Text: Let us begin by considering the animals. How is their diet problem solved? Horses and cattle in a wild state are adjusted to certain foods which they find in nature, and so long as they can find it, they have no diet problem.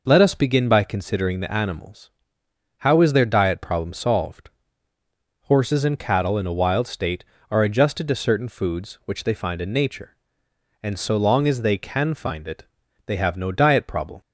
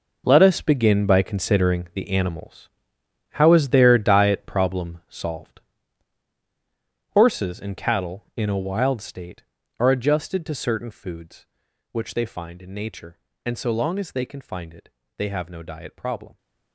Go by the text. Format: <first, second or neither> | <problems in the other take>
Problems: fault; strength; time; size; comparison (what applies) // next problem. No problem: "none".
first | gets quieter; strong; throughout; 12.5 dB